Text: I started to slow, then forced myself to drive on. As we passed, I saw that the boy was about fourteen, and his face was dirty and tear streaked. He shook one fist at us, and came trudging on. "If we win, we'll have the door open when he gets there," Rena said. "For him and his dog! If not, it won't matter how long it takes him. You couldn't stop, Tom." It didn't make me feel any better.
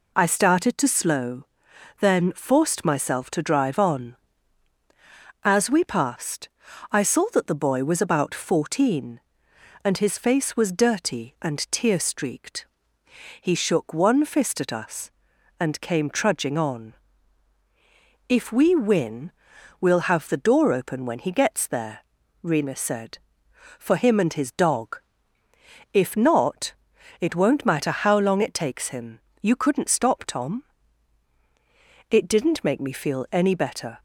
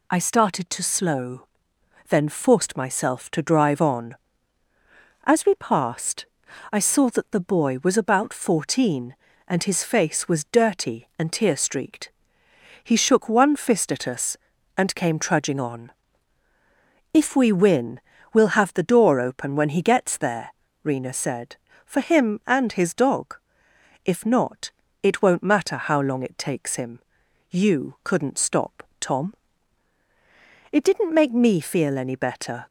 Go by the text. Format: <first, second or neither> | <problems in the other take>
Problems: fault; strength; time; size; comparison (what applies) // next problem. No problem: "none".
neither | none